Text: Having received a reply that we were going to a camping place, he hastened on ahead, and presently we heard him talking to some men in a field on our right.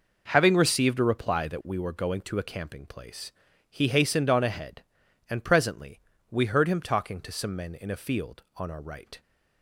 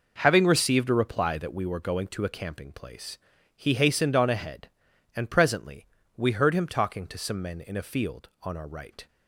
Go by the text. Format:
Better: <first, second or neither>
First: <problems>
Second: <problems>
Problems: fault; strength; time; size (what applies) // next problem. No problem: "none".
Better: neither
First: pauses between "presently" and "we"; slight; at 5.9 s; 0.30 s long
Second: pauses between "presently" and "we"; slight; at 5.8 s; 0.30 s long